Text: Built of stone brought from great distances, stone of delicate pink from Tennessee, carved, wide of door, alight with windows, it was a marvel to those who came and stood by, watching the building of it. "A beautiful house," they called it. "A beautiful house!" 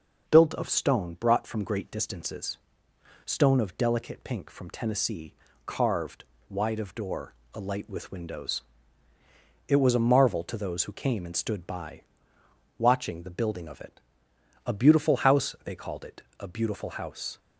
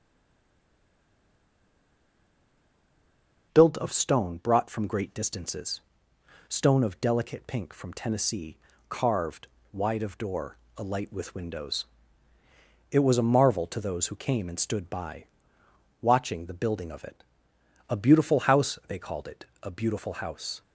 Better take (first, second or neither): first